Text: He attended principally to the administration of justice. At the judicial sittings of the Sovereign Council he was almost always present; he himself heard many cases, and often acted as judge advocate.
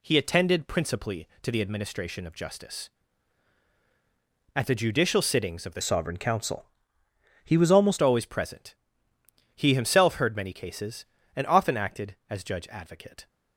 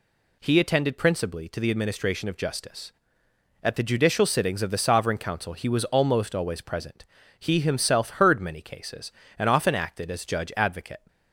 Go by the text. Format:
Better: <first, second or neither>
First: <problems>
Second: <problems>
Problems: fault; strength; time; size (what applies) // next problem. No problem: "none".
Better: second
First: changes voice from "Sovereign" to "almost"; from 5.8 to 7.9 s; 2.1 s long // pauses between "Council" and "he"; noticeable; at 6.6 s; 0.80 s long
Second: none